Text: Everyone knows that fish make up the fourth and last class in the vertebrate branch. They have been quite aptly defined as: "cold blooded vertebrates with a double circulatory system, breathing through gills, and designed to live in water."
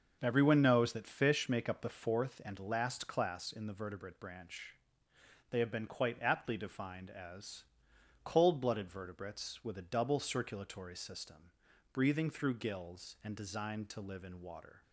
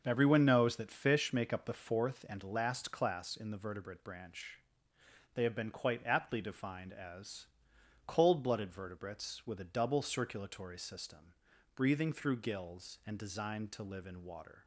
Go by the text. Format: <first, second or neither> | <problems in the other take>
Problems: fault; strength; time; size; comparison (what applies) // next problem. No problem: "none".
neither | starts louder than the rest; the same in both